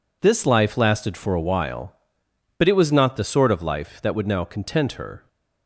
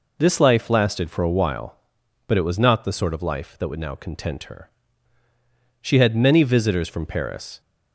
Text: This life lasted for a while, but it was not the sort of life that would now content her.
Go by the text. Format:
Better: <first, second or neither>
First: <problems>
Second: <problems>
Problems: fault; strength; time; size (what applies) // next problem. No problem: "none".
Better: first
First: none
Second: goes on to say "She had many visitors from Paris"; strong; from 5.8 s on; 1.7 s long